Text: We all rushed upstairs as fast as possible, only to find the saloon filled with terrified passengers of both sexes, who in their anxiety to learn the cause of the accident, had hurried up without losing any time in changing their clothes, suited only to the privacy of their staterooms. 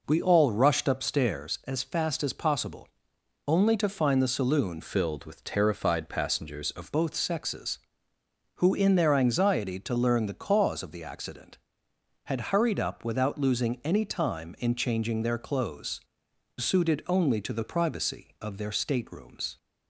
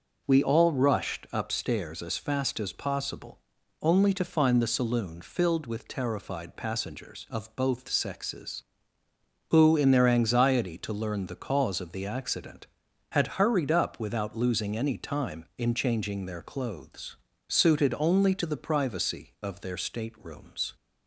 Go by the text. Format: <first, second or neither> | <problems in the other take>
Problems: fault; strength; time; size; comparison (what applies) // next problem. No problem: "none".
second | changes voice from "filled" to "of"; from 4.8 to 6.9 s; 2.1 s long